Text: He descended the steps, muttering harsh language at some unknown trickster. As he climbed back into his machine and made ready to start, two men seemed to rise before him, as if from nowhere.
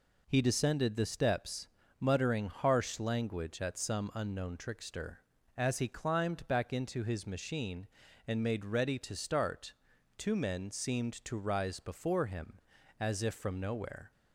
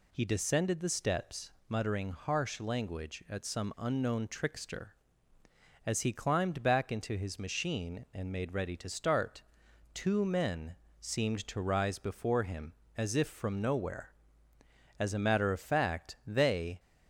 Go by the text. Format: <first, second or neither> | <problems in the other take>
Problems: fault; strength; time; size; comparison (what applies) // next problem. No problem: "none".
first | pauses between "men" and "seemed"; slight; at 10.7 s; 0.24 s long // goes on to say "As a matter of fact they"; strong; from 14.9 s on; 1.8 s long